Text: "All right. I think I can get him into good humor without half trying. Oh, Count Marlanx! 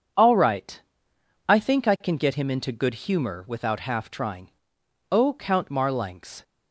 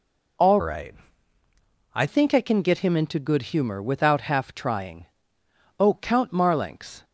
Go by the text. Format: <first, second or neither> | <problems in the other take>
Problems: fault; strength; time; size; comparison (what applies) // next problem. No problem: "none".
first | changes voice from "right" to "I"; from 0.6 to 2.0 s; 1.4 s long // pauses between "good" and "humor"; slight; at 3.4 s; 0.16 s long